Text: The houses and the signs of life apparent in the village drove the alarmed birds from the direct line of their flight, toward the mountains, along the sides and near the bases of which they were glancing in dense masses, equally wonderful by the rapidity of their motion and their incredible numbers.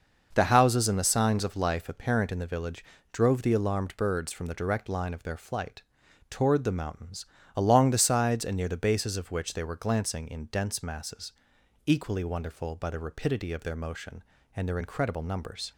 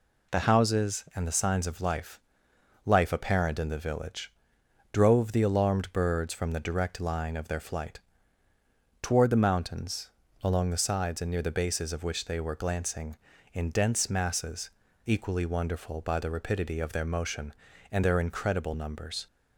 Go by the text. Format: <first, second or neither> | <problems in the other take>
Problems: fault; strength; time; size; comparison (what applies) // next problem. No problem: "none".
first | says "life" twice; at 2.8 s // pauses between "village" and "drove"; noticeable; at 4.3 s; 0.62 s long; slight in the first